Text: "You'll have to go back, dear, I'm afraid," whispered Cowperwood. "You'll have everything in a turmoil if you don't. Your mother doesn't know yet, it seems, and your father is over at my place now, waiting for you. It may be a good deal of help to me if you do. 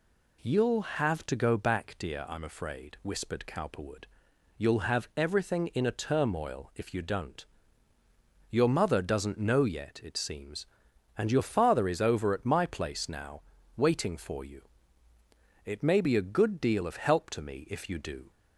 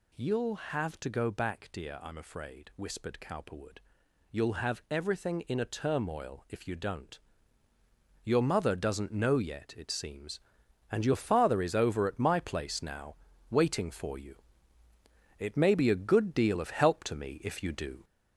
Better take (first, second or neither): first